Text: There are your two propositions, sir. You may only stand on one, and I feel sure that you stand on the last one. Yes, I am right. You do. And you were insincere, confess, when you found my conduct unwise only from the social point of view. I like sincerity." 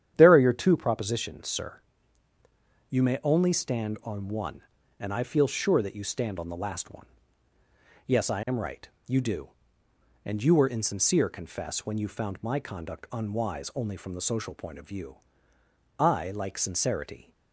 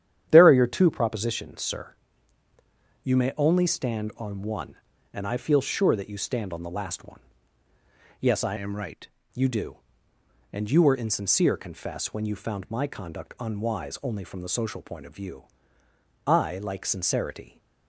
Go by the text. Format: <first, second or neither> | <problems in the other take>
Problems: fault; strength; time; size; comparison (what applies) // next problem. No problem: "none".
first | starts louder than the rest; strong; until 1.3 s; 9.5 dB; strong in the first // changes voice from "am" to "right"; from 8.5 to 9.0 s; 0.5 s long